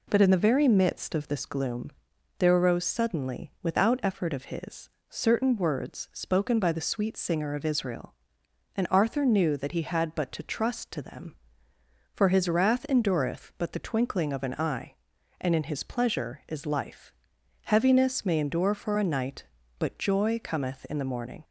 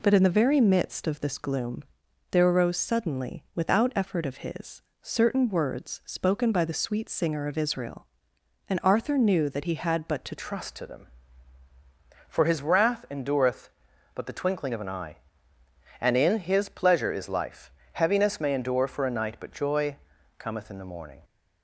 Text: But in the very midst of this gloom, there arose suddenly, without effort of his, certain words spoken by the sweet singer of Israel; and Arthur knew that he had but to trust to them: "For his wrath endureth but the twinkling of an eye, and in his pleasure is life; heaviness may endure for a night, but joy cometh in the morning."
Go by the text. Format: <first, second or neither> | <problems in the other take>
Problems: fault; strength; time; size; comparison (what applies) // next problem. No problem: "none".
first | changes voice at "trust"; from 10.3 s on; 10.8 s long // pauses between "joy" and "cometh"; at 19.9 s; 0.44 s long